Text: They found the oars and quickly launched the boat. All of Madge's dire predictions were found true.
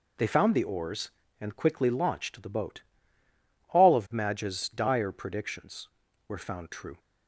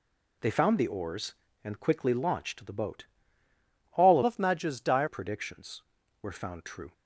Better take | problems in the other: first | changes voice from "of" to "dire"; from 4.2 to 5.0 s; 0.8 s long

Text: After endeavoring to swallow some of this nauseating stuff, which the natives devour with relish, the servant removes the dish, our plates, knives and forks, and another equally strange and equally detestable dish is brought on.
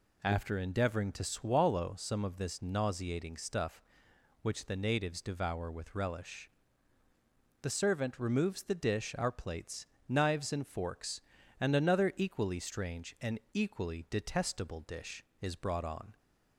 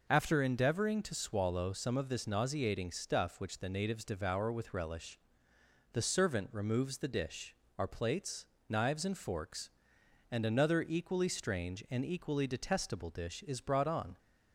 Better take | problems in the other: neither | none

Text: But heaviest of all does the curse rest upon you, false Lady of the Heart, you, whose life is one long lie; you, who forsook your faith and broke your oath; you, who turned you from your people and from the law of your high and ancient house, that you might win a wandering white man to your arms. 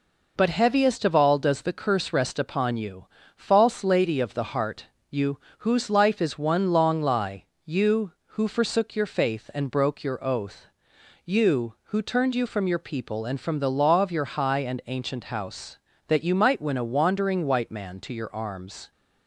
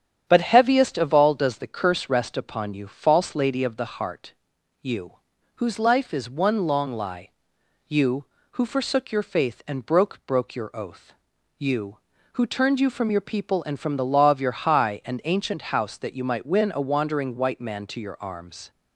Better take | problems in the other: first | starts louder than the rest; strong; until 1.2 s; 8.5 dB // says "broke" twice; at 10.2 s

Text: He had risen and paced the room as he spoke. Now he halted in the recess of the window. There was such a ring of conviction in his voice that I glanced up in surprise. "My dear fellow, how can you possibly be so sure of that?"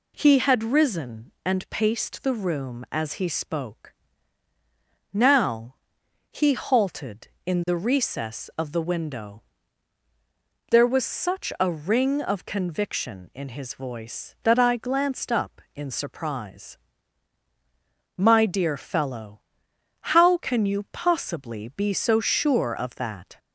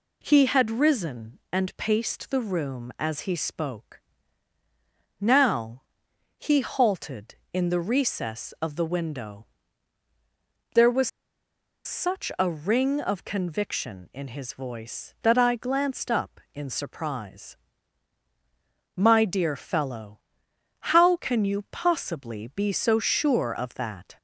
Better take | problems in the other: first | pauses between "Now" and "he"; noticeable; at 5.8 s; 0.56 s long; noticeable in the first // pauses between "was" and "such"; noticeable; at 11.0 s; 0.77 s long

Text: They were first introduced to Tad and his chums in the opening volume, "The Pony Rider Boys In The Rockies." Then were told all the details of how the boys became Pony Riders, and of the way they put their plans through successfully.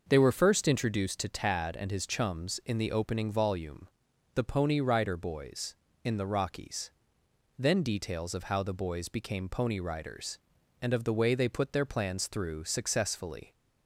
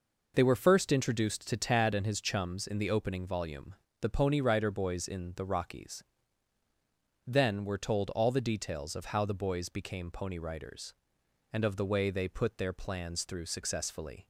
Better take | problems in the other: second | starts louder than the rest; noticeable; until 1.1 s; 6 dB // skips "were told all the"; at 7.8 s

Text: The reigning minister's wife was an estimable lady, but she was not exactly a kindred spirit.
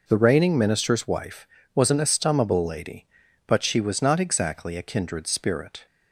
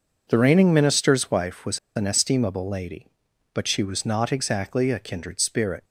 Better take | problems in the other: first | pauses between "was" and "an"; slight; at 1.7 s; 0.17 s long

